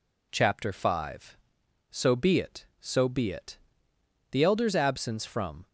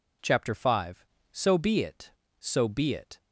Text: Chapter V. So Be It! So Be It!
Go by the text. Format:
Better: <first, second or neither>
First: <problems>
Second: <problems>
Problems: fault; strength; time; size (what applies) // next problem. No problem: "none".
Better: second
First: goes on to say "The elder's absence from"; from 4.3 s on; 1.3 s long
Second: none